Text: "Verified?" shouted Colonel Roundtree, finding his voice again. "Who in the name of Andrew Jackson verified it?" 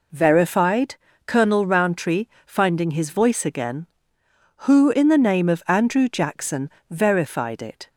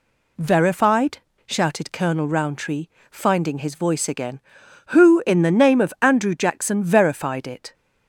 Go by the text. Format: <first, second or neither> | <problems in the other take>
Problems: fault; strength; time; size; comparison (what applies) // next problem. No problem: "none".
second | skips "shouted"; at 1.1 s // pauses between "Jackson" and "verified"; slight; at 6.6 s; 0.20 s long